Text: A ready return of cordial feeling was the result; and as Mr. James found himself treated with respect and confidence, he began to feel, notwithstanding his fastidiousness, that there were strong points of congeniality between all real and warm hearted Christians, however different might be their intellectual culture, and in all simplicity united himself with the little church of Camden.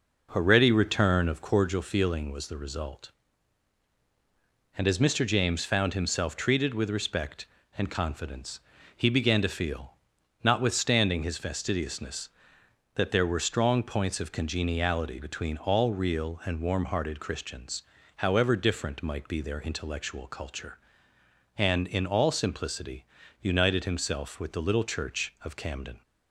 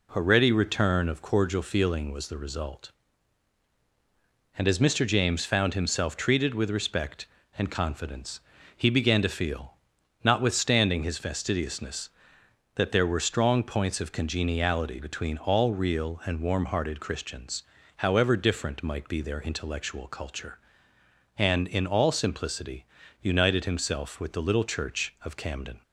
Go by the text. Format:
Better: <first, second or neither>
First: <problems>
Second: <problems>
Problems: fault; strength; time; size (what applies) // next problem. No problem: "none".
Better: second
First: starts louder than the rest; noticeable; until 1.8 s; 5 dB // pauses between "simplicity" and "united"; at 23.0 s; 0.38 s long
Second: pauses between "simplicity" and "united"; at 22.8 s; 0.38 s long